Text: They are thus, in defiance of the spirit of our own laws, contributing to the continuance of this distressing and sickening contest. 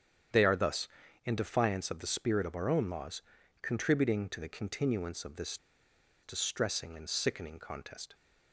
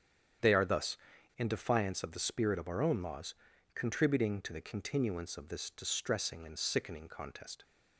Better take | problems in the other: second | starts louder than the rest; strong; until 1.6 s; 9 dB; strong in the second // pauses between "this" and "distressing"; noticeable; at 5.5 s; 0.66 s long

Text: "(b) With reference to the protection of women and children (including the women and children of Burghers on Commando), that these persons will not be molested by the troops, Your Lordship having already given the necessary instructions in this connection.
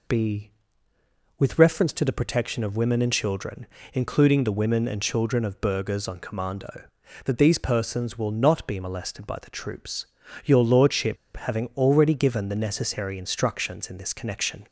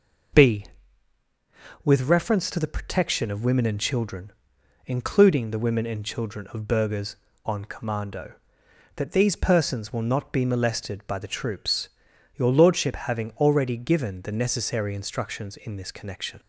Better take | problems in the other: second | pauses between "Lordship" and "having"; slight; at 11.1 s; 0.19 s long

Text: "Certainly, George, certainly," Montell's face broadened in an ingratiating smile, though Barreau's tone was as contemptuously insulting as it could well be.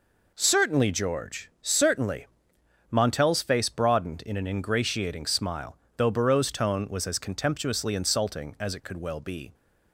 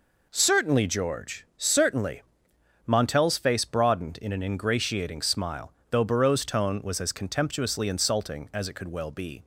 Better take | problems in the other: neither | none

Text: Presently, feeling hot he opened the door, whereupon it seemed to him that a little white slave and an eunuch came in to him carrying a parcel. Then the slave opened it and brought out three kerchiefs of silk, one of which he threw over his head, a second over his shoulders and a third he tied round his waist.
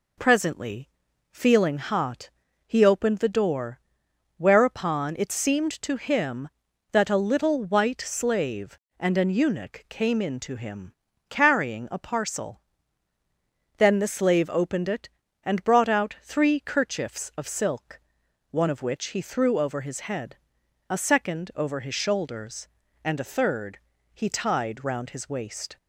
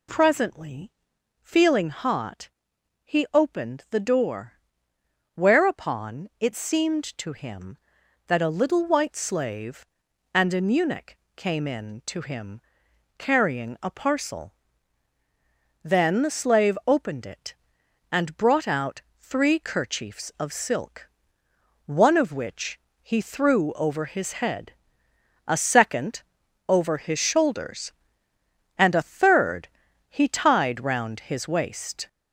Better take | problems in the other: first | gets louder; throughout; 3.5 dB // pauses between "hot" and "he"; noticeable; at 2.4 s; 0.54 s long; also in the first // pauses between "eunuch" and "came"; slight; at 11.1 s; 0.20 s long // pauses between "him" and "carrying"; noticeable; at 12.5 s; 0.60 s long; slight in the first // pauses between "out" and "three"; slight; at 19.0 s; 0.18 s long // pauses between "which" and "he"; slight; at 22.7 s; 0.22 s long // pauses between "second" and "over"; at 26.2 s; 0.44 s long // pauses between "third" and "he"; at 29.6 s; 0.42 s long; slight in the first

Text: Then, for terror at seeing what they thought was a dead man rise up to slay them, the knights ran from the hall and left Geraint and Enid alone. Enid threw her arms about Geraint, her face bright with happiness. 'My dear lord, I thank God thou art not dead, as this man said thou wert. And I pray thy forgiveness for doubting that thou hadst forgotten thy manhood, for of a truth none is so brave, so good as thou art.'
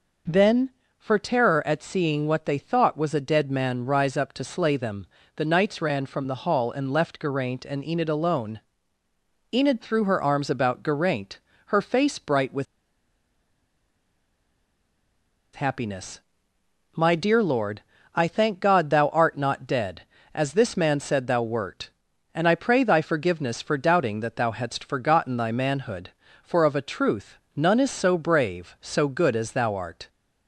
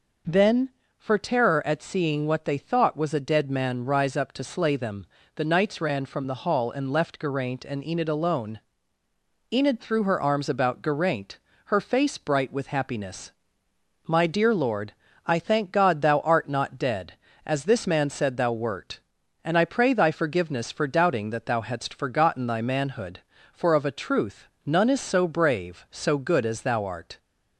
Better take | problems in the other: second | pauses between "with" and "happiness"; strong; at 12.6 s; 2.9 s long // pauses between "truth" and "none"; slight; at 27.3 s; 0.18 s long; slight in the second

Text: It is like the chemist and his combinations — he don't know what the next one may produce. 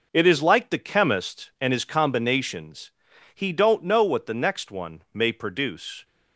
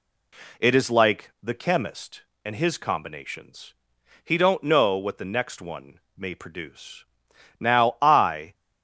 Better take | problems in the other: first | pauses between "one" and "may"; slight; at 5.9 s; 0.18 s long // goes on to say "Now I"; noticeable; from 7.5 s on; 0.94 s long

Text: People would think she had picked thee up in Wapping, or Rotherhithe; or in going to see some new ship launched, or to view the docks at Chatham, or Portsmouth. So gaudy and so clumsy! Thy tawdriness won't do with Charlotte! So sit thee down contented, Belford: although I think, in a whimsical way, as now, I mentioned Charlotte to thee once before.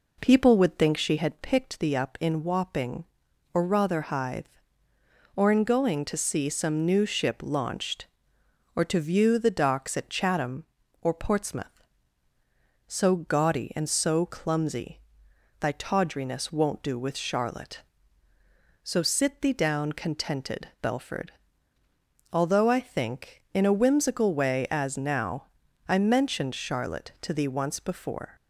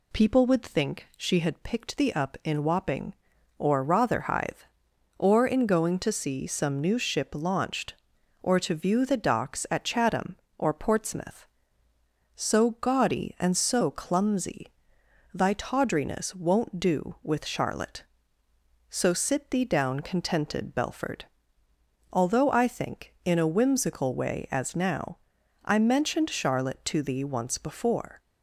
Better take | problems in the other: second | starts louder than the rest; until 1.4 s; 4 dB

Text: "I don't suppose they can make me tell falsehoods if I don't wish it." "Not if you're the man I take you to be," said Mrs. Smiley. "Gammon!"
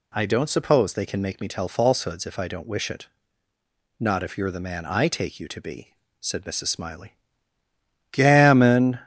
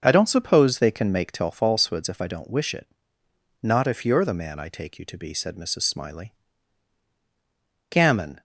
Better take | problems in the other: first | starts louder than the rest; until 1.0 s; 6.5 dB // skips "me"; at 1.3 s

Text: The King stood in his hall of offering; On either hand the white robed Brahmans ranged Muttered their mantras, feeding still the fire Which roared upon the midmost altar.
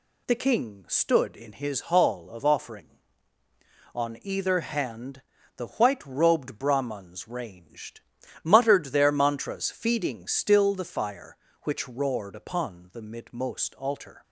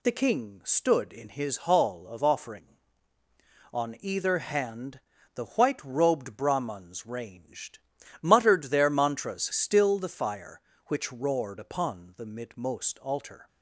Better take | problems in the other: first | pauses between "hand" and "the"; slight; at 5.0 s; 0.34 s long; slight in the first // pauses between "ranged" and "Muttered"; at 7.7 s; 0.42 s long; also in the first // skips "feeding"; at 9.4 s

